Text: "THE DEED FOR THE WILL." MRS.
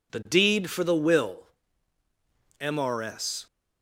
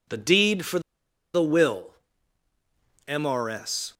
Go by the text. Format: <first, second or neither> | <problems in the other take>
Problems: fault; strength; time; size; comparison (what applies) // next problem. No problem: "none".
first | pauses between "FOR" and "THE"; noticeable; at 0.7 s; 0.54 s long